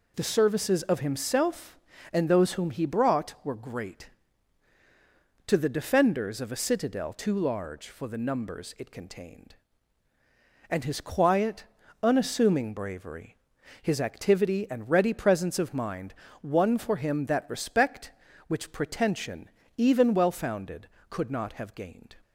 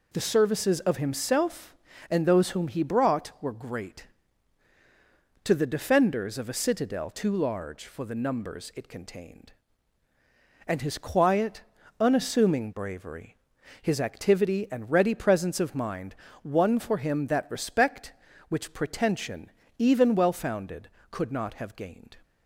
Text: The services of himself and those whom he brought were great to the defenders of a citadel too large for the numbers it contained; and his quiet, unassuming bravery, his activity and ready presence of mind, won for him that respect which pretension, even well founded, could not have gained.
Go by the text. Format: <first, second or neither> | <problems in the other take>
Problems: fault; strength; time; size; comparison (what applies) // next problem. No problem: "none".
neither | none